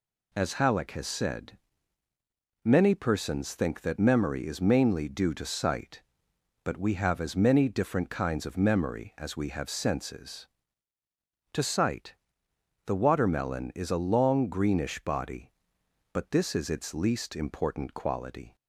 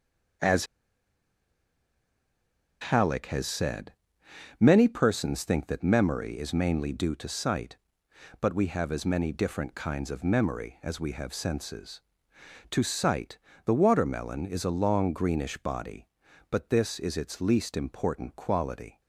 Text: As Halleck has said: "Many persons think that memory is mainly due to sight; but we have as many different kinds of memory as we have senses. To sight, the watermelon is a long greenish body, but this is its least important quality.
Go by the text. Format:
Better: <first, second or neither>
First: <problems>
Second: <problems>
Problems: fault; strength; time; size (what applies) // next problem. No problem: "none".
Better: first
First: none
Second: starts louder than the rest; until 3.5 s; 6.5 dB // pauses between "As" and "Halleck"; strong; at 0.6 s; 2.1 s long